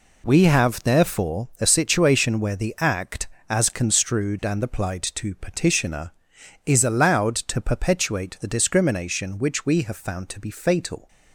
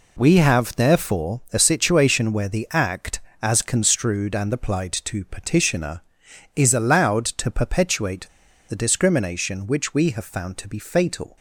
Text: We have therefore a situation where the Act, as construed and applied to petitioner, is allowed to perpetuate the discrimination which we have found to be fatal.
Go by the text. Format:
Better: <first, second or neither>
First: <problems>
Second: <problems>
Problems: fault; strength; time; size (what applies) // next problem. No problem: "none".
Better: first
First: none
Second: pauses between "perpetuate" and "the"; at 8.2 s; 0.42 s long